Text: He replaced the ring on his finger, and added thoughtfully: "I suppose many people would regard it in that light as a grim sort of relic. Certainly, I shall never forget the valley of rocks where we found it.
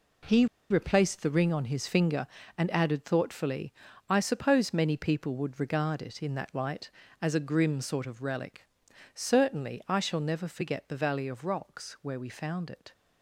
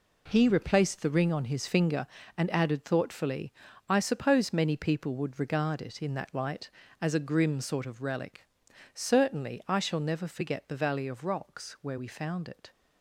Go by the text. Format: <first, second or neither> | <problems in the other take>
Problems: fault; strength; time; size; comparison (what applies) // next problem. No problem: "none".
second | pauses between "He" and "replaced"; slight; at 0.4 s; 0.24 s long